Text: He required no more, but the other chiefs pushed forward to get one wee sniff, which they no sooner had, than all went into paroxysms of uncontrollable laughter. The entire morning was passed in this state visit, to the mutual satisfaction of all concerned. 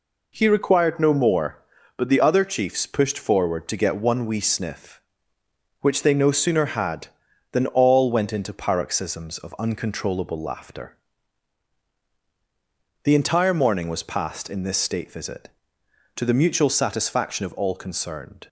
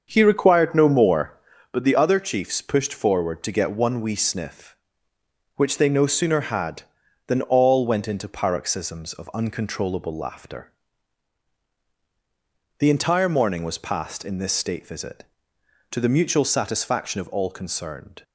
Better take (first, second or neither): first